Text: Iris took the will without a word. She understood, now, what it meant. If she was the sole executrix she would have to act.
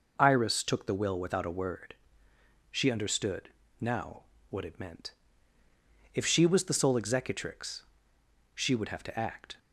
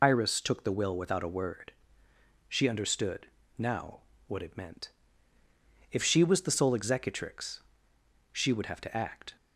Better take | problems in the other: first | loses the start of "Iris"; at 0.0 s; 65 ms // pauses between "executrix" and "she"; noticeable; at 7.5 s; 0.76 s long; noticeable in the first

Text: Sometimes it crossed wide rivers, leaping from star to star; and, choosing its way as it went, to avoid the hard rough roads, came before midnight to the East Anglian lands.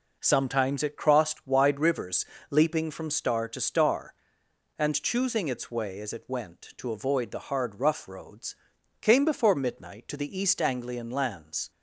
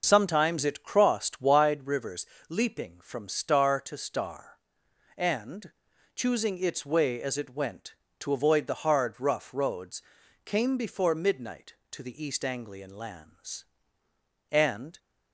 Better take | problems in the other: first | goes on to say "And"; slight; from 14.5 s on; 0.48 s long

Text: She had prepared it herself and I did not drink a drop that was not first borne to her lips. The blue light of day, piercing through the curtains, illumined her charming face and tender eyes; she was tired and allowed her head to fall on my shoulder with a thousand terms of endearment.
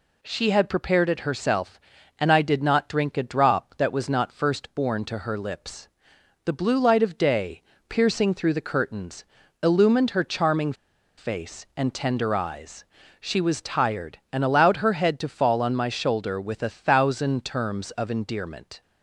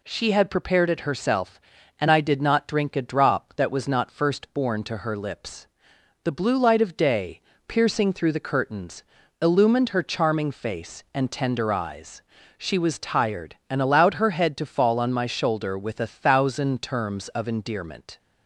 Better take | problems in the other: second | pauses between "charming" and "face"; at 10.7 s; 0.44 s long

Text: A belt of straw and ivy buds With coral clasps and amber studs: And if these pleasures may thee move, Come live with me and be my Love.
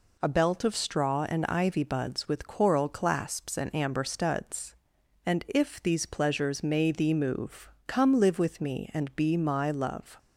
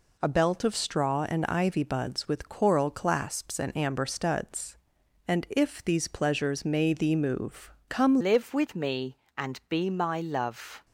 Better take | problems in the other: first | changes voice at "live"; from 8.2 s on; 2.6 s long

